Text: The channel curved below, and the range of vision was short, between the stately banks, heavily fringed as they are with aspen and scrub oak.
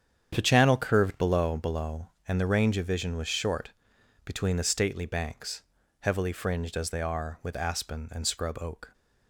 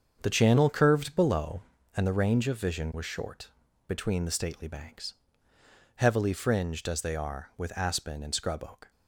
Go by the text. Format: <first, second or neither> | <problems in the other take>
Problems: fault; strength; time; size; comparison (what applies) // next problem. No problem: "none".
second | starts louder than the rest; strong; until 1.3 s; 8.5 dB; strong in the second // says "below" twice; at 1.5 s